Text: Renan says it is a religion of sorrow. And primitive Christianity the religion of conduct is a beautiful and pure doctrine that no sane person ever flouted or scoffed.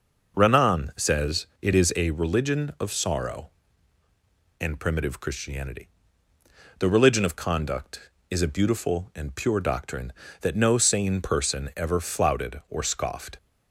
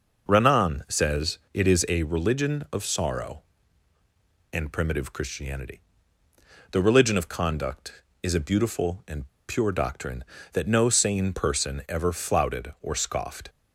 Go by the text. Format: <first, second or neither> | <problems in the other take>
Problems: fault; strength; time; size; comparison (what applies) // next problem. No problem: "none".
first | pauses between "says" and "it"; slight; at 1.3 s; 0.16 s long; slight in the first // pauses between "Christianity" and "the"; noticeable; at 5.7 s; 0.92 s long; noticeable in the first // pauses between "and" and "pure"; slight; at 9.2 s; 0.20 s long